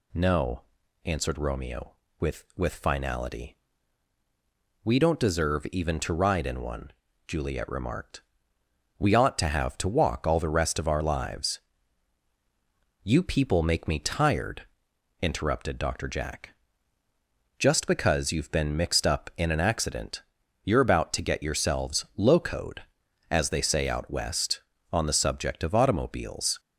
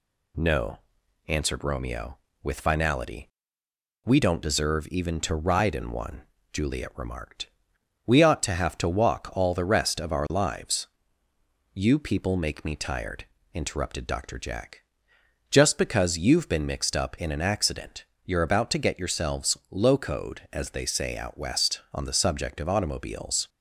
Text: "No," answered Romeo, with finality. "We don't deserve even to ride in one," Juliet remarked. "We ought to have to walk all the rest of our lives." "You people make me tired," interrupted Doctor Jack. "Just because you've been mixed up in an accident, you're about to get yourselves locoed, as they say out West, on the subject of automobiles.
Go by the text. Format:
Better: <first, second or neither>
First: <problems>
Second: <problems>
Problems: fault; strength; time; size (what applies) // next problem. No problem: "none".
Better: second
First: says "with" twice; at 2.5 s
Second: none